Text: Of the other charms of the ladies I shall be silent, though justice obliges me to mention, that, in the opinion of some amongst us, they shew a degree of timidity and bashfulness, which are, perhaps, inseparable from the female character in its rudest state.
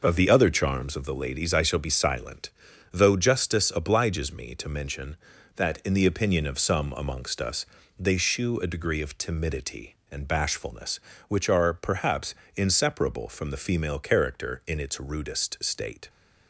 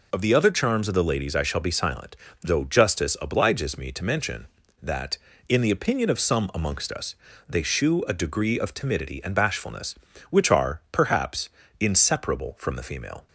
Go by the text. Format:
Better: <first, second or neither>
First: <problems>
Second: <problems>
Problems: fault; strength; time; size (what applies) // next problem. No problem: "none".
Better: first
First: none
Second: stops before "character in its rudest state"; at 13.2 s